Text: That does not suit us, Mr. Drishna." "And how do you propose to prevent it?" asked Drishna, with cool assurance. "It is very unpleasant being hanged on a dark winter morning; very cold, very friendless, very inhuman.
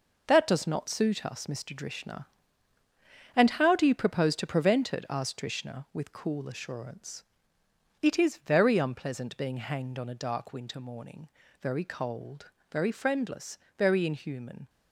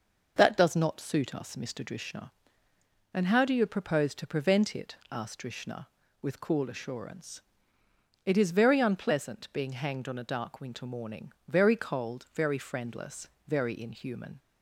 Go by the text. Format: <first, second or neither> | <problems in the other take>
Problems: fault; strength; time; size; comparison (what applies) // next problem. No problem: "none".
second | gets quieter; strong; throughout; 7 dB